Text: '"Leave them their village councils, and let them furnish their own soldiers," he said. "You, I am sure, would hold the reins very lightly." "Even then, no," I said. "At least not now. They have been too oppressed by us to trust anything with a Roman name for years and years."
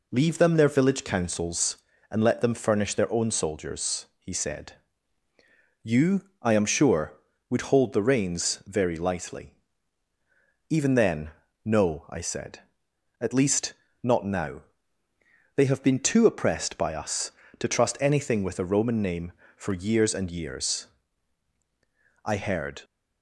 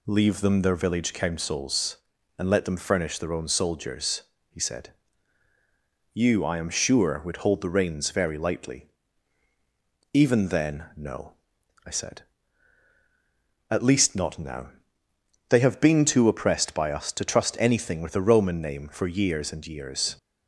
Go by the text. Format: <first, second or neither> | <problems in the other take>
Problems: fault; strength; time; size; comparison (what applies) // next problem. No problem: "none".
second | pauses between "least" and "not"; slight; at 13.7 s; 0.28 s long // goes on to say "I heard"; from 22.2 s on; 0.58 s long